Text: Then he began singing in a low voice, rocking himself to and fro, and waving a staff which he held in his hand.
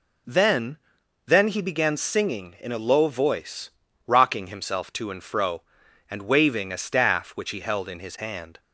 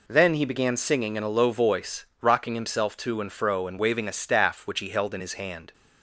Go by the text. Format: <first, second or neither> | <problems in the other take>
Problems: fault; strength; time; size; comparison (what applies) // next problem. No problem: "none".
second | says "Then" twice; at 1.2 s